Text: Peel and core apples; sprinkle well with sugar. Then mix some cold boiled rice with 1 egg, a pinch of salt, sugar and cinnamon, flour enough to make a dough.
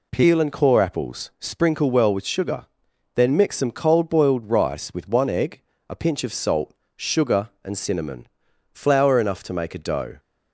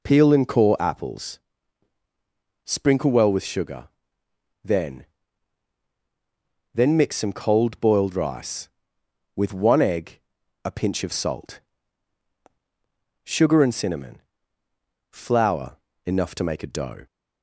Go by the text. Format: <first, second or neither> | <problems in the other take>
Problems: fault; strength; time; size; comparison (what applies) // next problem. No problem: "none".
first | says "Then" twice; at 6.7 s // pauses between "flour" and "enough"; slight; at 15.7 s; 0.28 s long